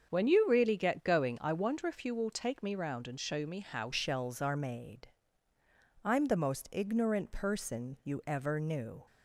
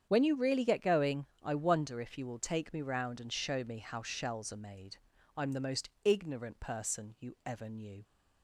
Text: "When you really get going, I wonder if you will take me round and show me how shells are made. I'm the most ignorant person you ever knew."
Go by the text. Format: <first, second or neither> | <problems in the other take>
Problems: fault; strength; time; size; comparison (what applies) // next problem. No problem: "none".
second | starts louder than the rest; until 1.1 s; 7 dB; strong in the second // changes voice at "shells"; from 3.9 s on; 5.1 s long